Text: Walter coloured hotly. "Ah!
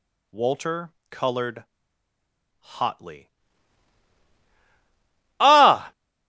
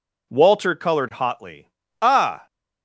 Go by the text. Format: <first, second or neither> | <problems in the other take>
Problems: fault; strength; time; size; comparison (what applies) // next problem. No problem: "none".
second | pauses between "Walter" and "coloured"; slight; at 0.9 s; 0.18 s long // pauses between "coloured" and "hotly"; noticeable; at 1.6 s; 0.94 s long